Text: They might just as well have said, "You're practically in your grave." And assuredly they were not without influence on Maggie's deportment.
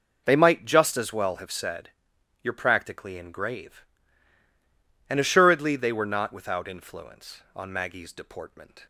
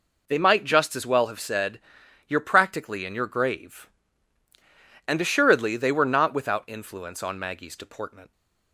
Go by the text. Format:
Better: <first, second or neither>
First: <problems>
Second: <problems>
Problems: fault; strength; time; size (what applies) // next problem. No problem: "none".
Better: second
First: skips "your"; at 3.3 s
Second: none